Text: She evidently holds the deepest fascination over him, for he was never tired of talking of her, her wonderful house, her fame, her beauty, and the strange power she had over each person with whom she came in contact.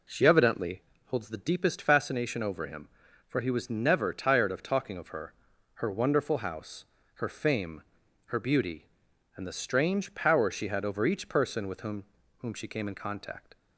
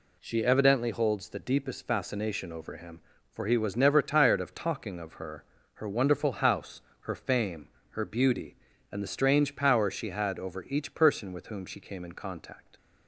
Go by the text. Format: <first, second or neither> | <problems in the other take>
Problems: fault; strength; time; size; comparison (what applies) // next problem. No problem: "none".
second | pauses between "evidently" and "holds"; slight; at 0.8 s; 0.28 s long // says "whom" twice; at 12.3 s